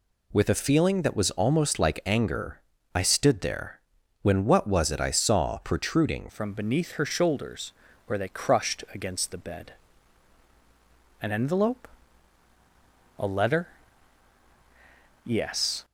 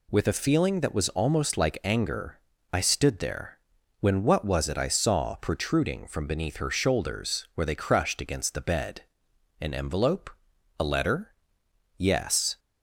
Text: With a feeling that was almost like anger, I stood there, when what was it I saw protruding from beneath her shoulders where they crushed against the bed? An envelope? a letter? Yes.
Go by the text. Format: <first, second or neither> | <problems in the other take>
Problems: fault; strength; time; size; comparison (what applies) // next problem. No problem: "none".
second | changes voice at "from"; from 6.3 s on; 9.5 s long // pauses between "shoulders" and "where"; slight; at 7.7 s; 0.32 s long